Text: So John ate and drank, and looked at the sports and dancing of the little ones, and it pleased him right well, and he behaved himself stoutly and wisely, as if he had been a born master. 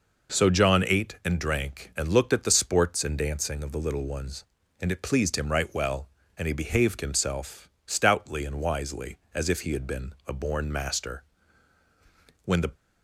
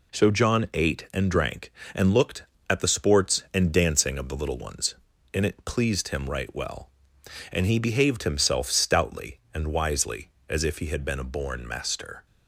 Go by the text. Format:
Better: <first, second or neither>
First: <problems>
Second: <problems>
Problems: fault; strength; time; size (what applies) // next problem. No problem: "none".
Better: second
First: pauses between "himself" and "stoutly"; slight; at 7.6 s; 0.16 s long // pauses between "been" and "a"; slight; at 10.1 s; 0.16 s long // goes on to say "When the"; slight; from 12.4 s on; 0.26 s long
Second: none